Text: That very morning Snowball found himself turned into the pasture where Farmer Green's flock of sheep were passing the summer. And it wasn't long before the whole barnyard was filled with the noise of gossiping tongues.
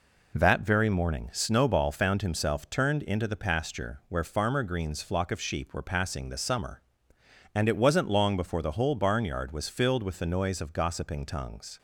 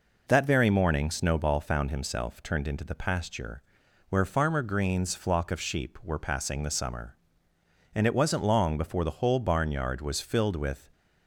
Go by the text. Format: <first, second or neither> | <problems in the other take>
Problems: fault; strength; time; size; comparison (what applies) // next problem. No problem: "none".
first | pauses between "pasture" and "where"; noticeable; at 3.6 s; 0.48 s long // stops before "the noise of gossiping tongues"; at 10.9 s